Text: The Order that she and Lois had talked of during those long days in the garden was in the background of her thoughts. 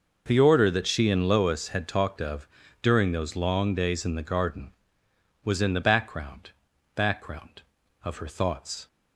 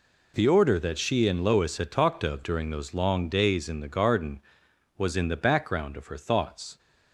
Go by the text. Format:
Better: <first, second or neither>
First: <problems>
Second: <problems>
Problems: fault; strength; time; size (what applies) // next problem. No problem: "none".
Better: second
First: pauses between "of" and "during"; slight; at 2.4 s; 0.34 s long // says "background" twice; at 6.9 s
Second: none